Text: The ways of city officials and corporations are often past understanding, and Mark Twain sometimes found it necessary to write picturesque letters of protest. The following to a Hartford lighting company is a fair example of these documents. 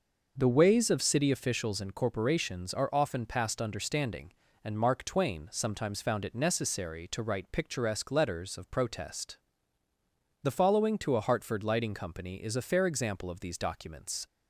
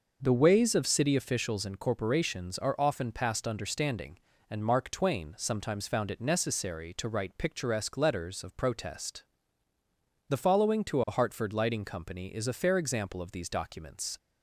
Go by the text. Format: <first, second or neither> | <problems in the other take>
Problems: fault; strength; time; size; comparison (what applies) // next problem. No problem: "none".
neither | none